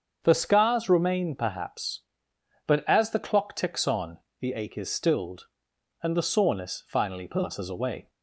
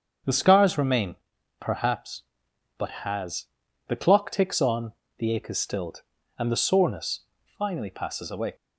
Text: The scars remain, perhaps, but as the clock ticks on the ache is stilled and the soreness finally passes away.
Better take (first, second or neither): first